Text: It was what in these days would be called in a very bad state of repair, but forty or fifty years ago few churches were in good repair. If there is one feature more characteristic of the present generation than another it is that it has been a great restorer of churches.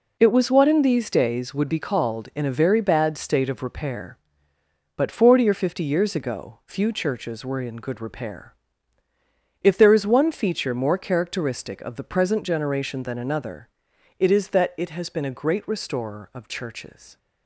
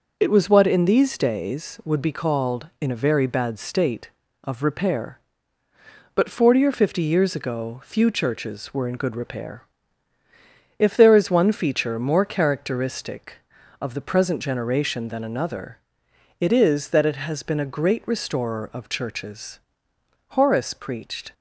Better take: first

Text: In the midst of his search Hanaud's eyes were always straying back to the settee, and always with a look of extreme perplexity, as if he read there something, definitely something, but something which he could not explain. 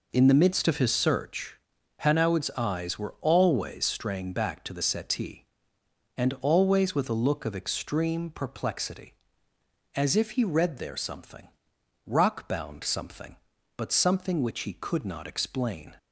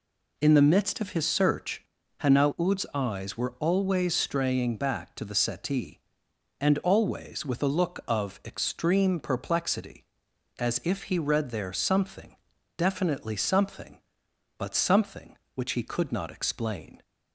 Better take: second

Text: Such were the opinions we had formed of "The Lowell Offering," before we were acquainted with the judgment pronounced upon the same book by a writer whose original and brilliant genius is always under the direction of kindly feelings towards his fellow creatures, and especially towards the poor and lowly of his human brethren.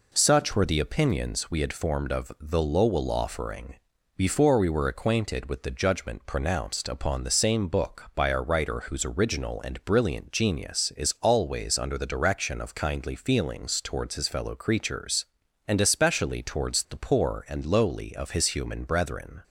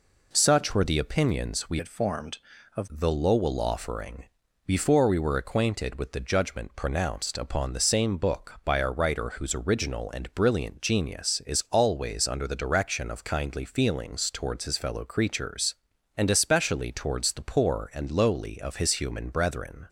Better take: first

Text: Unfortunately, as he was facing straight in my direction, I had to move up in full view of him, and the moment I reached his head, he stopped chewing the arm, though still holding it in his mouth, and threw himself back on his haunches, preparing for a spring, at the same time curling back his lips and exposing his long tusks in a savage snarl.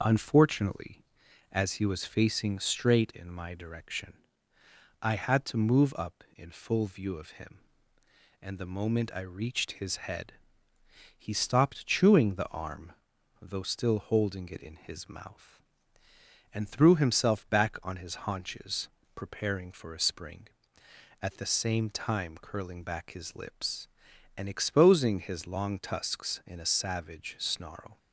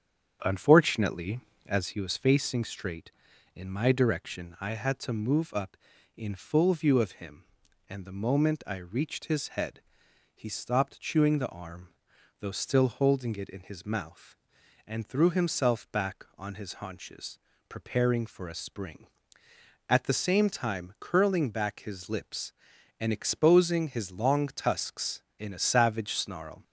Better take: first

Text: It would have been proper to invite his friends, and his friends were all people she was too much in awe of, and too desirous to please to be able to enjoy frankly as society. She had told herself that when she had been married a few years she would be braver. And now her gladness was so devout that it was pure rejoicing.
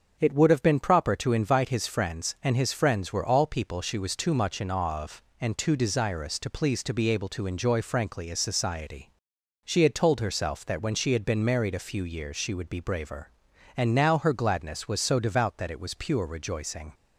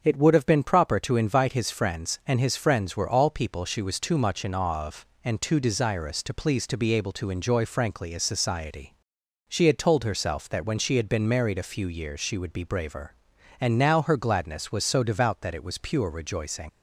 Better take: first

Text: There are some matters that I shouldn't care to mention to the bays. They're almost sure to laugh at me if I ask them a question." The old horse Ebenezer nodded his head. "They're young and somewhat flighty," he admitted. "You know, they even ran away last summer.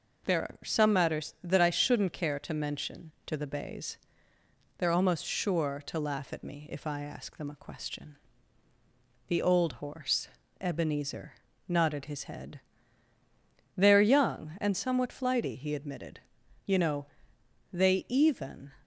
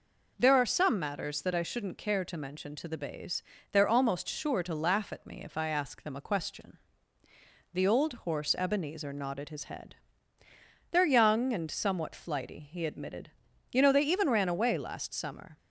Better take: second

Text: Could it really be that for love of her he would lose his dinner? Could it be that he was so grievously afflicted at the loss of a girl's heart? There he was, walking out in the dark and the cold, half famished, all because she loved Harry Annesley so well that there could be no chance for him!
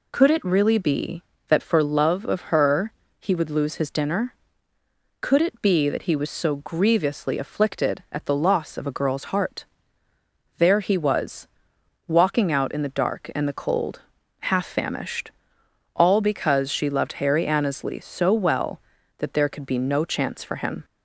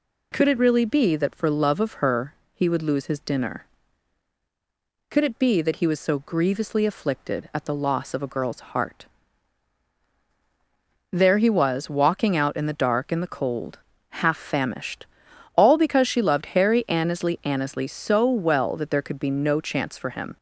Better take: first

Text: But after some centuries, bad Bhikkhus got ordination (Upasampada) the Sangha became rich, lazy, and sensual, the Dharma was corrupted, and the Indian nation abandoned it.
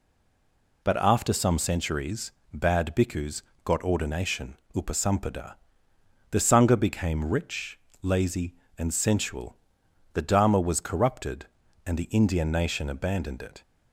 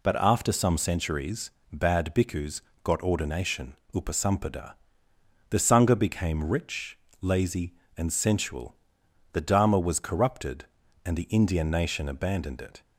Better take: second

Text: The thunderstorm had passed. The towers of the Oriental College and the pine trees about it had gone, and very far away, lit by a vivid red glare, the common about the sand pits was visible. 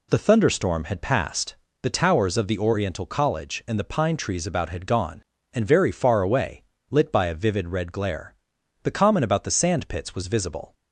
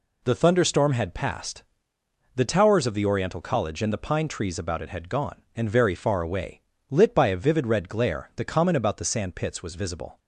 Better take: second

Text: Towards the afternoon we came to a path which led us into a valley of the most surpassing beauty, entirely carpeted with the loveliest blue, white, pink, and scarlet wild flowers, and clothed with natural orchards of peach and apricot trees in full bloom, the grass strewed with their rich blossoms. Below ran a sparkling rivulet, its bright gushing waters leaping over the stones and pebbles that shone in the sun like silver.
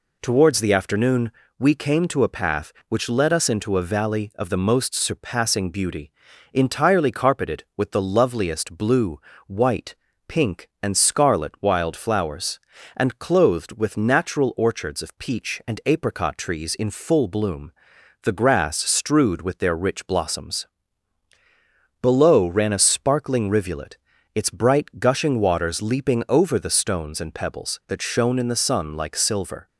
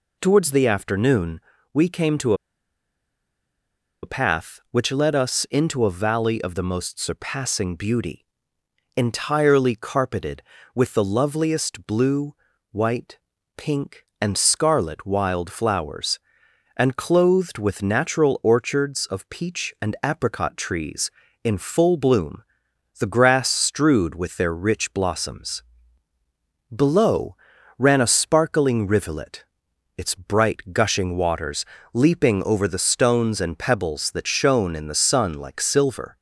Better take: first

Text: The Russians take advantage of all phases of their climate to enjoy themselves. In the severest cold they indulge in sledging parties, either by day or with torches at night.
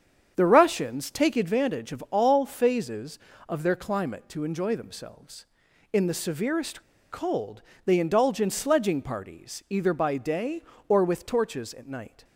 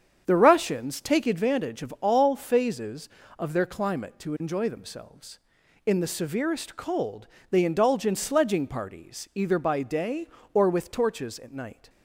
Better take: second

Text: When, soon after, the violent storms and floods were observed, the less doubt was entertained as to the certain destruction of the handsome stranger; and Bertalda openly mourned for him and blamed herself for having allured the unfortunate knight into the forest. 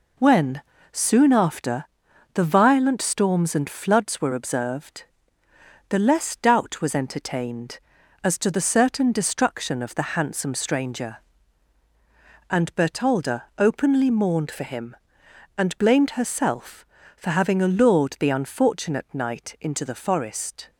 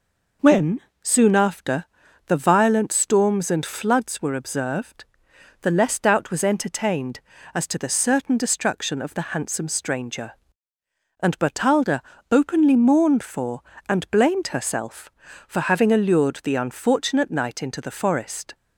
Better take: first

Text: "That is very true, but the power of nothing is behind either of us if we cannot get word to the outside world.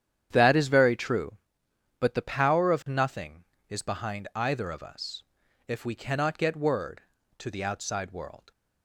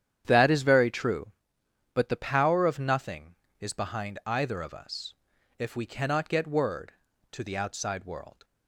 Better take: neither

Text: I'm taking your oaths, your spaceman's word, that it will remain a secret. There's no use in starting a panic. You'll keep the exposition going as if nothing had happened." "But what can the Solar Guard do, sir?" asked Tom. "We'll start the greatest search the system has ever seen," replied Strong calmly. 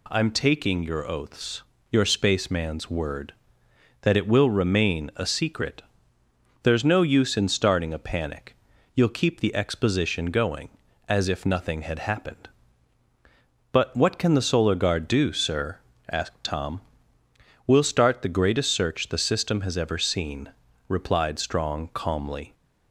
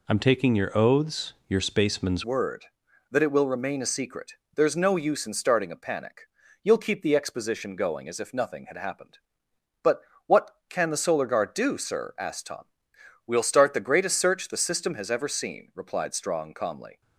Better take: first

